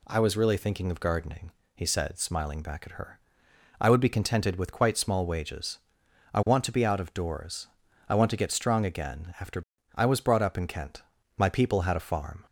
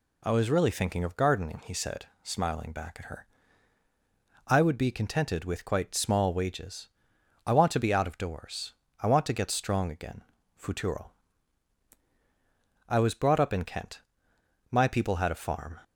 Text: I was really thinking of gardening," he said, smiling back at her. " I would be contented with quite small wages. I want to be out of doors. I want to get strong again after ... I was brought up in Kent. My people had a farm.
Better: first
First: none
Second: says "futuro" for "after"; at 10.5 s

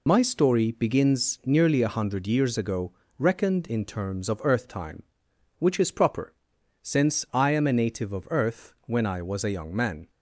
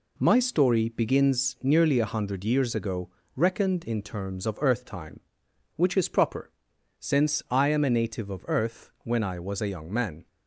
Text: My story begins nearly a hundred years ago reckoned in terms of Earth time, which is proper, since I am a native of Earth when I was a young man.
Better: second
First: loses the start of "My"; at 0.0 s; 75 ms // pauses between "ago" and "reckoned"; slight; at 2.9 s; 0.24 s long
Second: pauses between "ago" and "reckoned"; slight; at 3.1 s; 0.24 s long

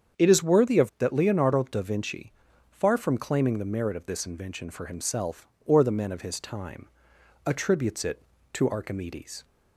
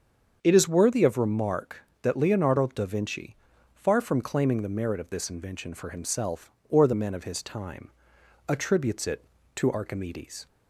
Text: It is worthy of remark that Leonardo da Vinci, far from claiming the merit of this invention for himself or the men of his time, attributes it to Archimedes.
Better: second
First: starts louder than the rest; strong; until 1.2 s; 7.5 dB // skips "remark"; at 0.9 s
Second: starts louder than the rest; until 1.4 s; 7 dB

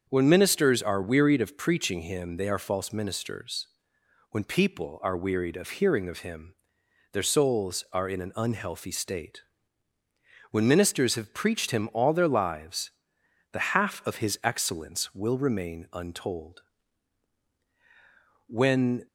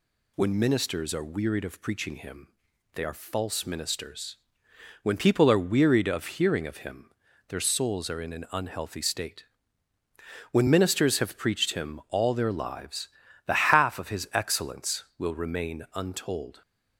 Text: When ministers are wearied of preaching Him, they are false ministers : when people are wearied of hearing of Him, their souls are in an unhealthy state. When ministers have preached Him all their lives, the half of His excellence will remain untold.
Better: second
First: starts louder than the rest; until 1.1 s; 7 dB // goes on to say "When"; from 18.4 s on; 0.58 s long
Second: none

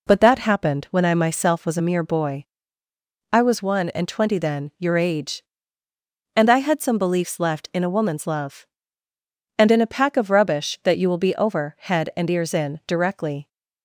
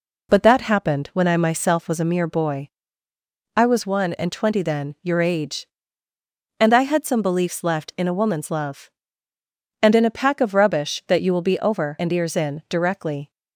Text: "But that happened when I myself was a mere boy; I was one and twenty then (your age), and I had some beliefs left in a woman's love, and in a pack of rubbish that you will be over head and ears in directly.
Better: first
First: none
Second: skips "head"; at 11.9 s

